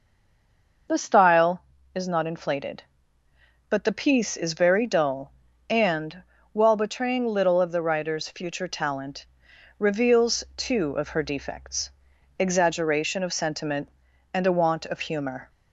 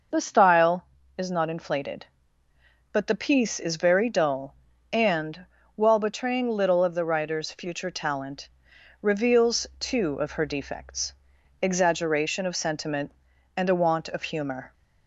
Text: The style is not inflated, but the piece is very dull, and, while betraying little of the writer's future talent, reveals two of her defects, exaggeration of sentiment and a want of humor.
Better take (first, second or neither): second